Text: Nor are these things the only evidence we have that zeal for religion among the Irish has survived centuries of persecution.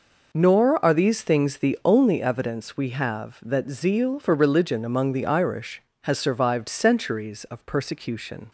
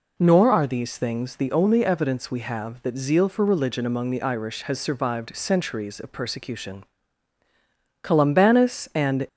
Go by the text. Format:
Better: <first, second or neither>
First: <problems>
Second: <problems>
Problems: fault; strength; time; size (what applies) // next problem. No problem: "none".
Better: first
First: none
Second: goes on to say "Columbanus and"; noticeable; from 8.0 s on; 1.2 s long